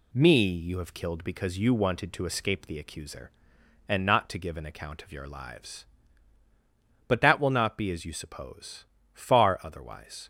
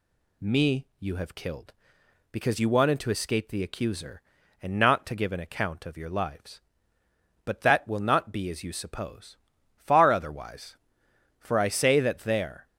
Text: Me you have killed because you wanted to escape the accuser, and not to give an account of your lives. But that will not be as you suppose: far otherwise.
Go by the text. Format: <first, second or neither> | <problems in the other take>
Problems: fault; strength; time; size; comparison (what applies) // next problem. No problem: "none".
first | goes on to say "For I say that there"; noticeable; from 11.4 s on; 1.2 s long